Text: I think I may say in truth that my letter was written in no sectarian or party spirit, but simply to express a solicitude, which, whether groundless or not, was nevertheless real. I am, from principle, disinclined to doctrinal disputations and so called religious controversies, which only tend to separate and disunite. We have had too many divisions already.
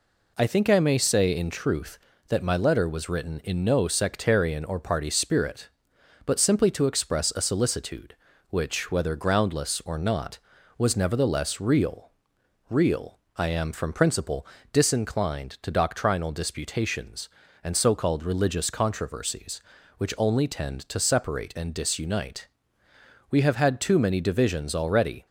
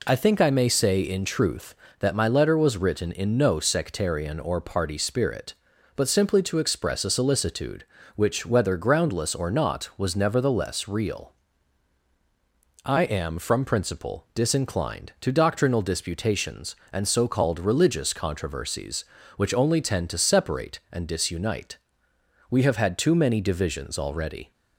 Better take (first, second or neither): second